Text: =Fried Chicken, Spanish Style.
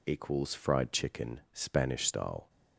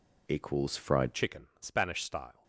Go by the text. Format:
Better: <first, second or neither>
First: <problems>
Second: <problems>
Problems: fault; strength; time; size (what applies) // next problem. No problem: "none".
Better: first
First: none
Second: changes voice at "Chicken"; from 1.1 s on; 1.3 s long